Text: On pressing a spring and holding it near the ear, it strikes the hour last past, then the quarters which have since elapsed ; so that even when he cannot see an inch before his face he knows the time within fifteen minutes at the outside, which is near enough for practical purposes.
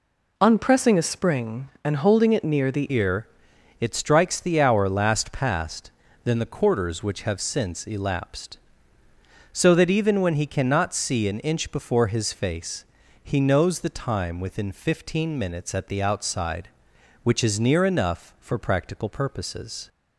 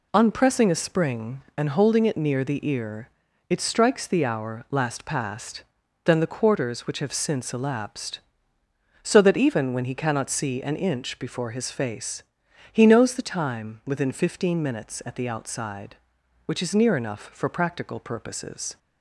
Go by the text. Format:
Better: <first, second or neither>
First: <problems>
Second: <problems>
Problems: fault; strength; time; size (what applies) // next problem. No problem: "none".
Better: second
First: changes voice at "ear"; from 2.9 s on; 16.9 s long // pauses between "face" and "he"; at 12.8 s; 0.40 s long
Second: pauses between "face" and "he"; noticeable; at 12.2 s; 0.50 s long